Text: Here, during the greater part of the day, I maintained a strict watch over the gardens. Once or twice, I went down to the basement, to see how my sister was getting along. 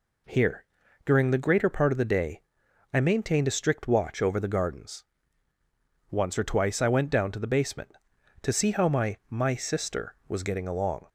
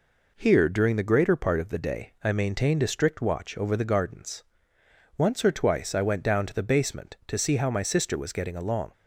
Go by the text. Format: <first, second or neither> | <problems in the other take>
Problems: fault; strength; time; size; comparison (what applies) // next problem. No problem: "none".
second | says "my" twice; at 9.2 s